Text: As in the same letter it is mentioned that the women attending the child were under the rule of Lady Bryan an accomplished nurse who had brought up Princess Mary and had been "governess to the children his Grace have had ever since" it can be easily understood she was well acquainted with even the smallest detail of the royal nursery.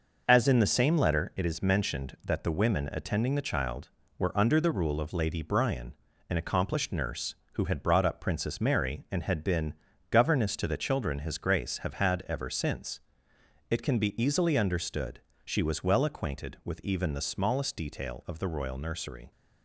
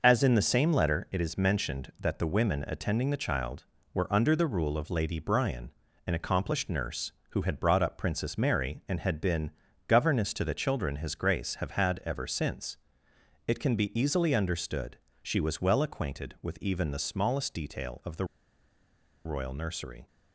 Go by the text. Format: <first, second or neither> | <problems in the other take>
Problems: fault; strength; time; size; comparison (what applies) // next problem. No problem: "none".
first | pauses between "Bryan" and "an"; slight; at 5.7 s; 0.36 s long; slight in the first // pauses between "been" and "governess"; at 9.5 s; 0.38 s long; also in the first // pauses between "since" and "it"; noticeable; at 12.7 s; 0.72 s long; noticeable in the first // pauses between "understood" and "she"; slight; at 14.9 s; 0.22 s long; slight in the first // pauses between "the" and "royal"; at 18.2 s; 1.0 s long